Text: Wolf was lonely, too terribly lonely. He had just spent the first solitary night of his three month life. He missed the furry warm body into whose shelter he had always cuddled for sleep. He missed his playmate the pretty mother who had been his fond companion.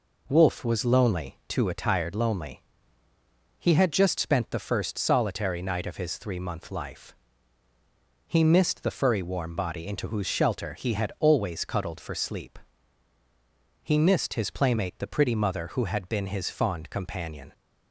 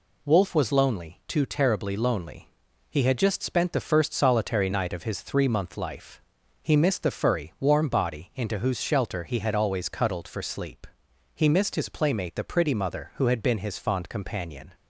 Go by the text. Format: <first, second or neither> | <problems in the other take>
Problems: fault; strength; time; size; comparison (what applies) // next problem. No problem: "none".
second | says "attired" for "terribly"; at 1.6 s